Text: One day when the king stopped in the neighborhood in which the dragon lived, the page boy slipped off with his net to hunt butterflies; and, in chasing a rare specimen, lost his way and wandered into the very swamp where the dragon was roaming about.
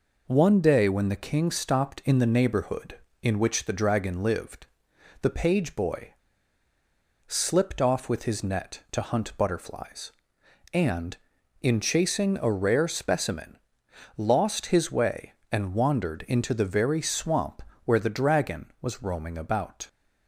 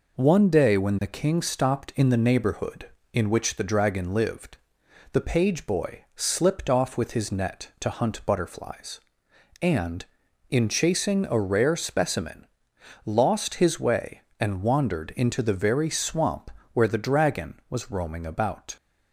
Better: second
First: pauses between "boy" and "slipped"; at 6.1 s; 1.1 s long // pauses between "swamp" and "where"; slight; at 17.5 s; 0.26 s long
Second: pauses between "swamp" and "where"; slight; at 16.4 s; 0.26 s long

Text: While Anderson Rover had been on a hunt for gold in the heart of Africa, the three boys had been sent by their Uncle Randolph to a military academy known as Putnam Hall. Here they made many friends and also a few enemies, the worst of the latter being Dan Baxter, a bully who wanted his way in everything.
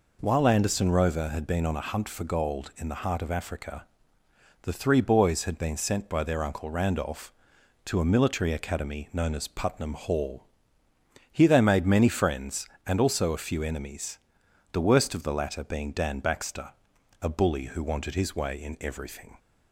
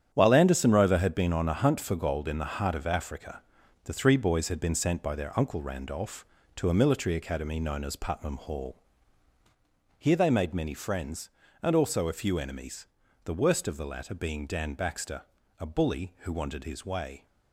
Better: first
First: none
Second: starts louder than the rest; strong; until 1.1 s; 9.5 dB // stops before "in everything"; at 17.2 s

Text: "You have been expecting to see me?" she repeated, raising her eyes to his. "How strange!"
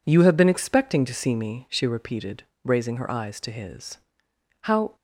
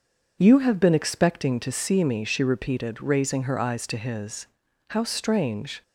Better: second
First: stops before "strange"; at 4.9 s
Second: none

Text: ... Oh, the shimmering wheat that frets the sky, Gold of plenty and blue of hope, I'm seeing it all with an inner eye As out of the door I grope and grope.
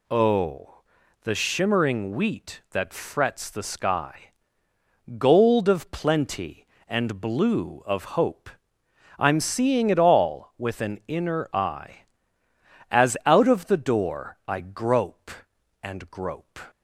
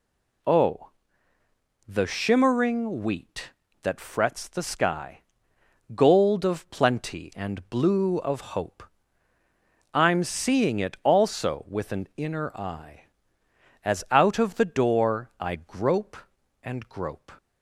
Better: first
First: none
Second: pauses between "of" and "hope"; slight; at 8.3 s; 0.16 s long // says "also" for "all"; at 11.0 s

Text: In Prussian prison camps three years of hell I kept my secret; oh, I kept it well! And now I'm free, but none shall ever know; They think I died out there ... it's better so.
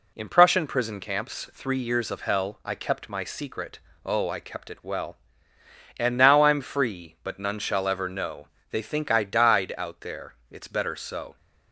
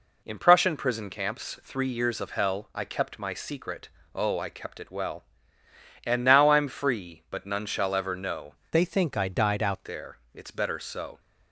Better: first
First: none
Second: changes voice from "They" to "out"; from 8.7 to 9.8 s; 1.1 s long

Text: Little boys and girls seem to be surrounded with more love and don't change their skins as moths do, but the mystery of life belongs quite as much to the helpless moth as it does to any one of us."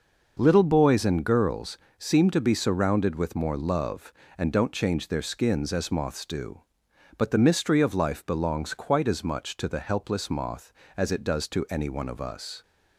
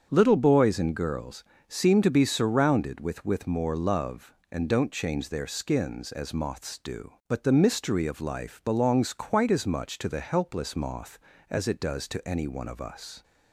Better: first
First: pauses between "girls" and "seem"; slight; at 1.7 s; 0.20 s long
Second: starts louder than the rest; strong; until 1.1 s; 7.5 dB // pauses between "girls" and "seem"; slight; at 1.4 s; 0.26 s long // says "with" twice; at 3.2 s

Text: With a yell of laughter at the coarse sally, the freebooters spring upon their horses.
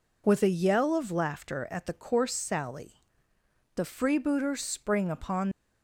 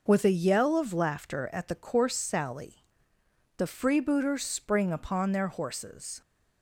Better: second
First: stops before "their horses"; at 5.5 s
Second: none

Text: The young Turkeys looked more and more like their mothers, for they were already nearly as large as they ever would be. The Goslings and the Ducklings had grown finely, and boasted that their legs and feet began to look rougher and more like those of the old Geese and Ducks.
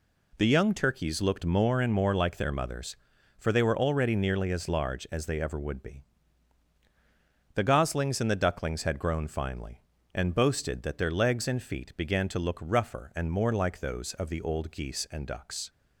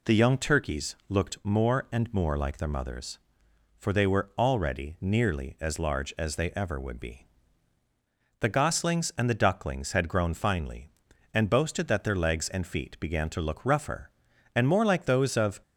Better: first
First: none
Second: stops before "the old Geese and Ducks"; at 15.6 s

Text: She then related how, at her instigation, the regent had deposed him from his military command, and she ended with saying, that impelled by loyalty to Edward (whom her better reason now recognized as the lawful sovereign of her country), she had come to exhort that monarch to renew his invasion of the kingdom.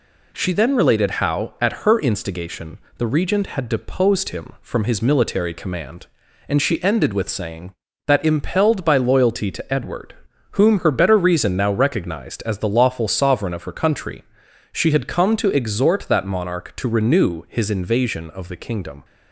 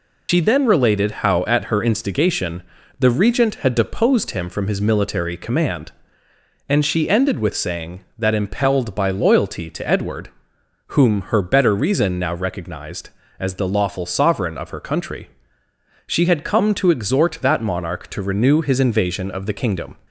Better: first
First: none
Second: loses the start of "She"; at 0.2 s; 85 ms

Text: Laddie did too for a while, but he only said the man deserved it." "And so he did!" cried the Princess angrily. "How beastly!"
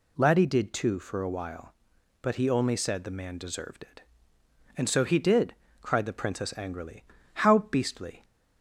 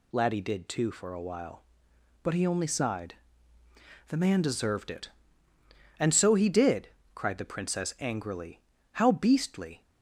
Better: first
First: none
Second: says "sighed" for "said"; at 2.6 s

